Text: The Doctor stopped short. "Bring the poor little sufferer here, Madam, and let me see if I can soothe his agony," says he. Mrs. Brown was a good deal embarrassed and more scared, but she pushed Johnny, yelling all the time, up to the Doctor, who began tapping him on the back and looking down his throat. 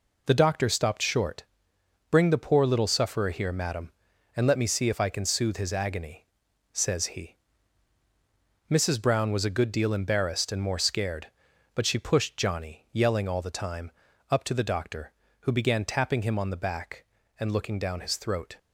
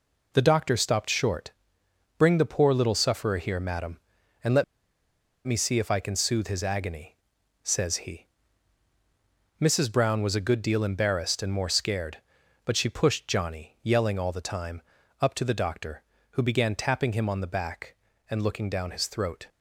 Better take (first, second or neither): first